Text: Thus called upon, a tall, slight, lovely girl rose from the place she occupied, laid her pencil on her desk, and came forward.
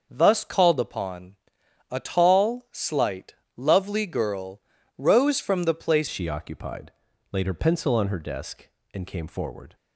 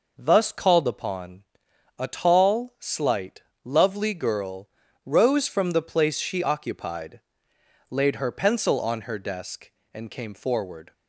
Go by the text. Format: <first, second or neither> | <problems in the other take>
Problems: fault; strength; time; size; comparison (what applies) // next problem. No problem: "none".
second | starts louder than the rest; until 1.1 s; 6.5 dB // pauses between "girl" and "rose"; slight; at 4.6 s; 0.36 s long; slight in the second // changes voice at "she"; from 6.0 s on; 3.7 s long